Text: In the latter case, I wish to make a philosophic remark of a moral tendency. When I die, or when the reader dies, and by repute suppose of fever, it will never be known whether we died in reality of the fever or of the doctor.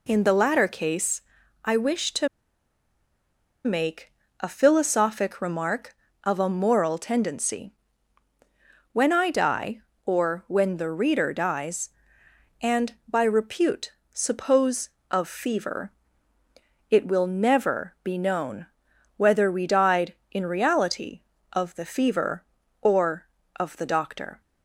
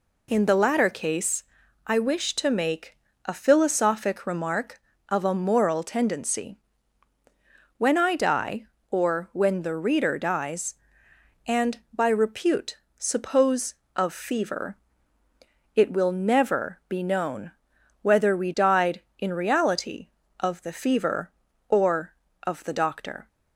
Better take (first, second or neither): second